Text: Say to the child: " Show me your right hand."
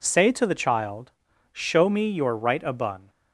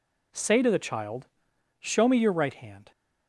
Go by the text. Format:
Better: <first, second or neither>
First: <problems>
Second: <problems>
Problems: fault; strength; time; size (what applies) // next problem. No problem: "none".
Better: second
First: says "abun" for "hand"; at 2.6 s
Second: none